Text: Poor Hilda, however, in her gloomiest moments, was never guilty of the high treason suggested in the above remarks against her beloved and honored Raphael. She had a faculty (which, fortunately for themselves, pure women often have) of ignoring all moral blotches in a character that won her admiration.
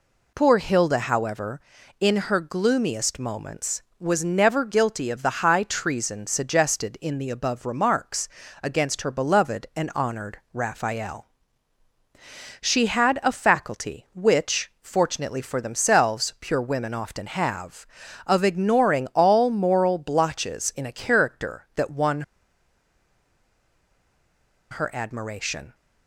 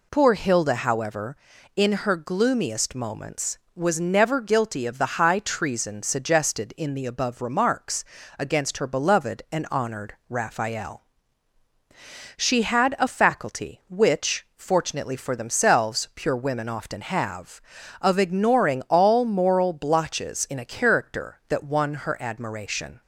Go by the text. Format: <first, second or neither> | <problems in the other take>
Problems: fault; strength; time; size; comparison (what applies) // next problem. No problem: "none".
second | pauses between "remarks" and "against"; slight; at 8.2 s; 0.34 s long; slight in the second // pauses between "won" and "her"; strong; at 22.2 s; 2.4 s long